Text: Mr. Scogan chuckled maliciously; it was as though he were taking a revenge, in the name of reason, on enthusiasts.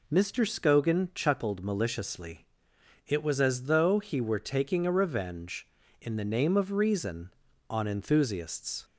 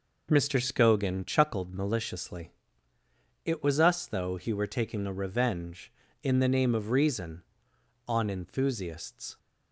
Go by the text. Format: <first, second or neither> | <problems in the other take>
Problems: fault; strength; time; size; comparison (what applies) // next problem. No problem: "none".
first | says "us" for "as"; at 3.7 s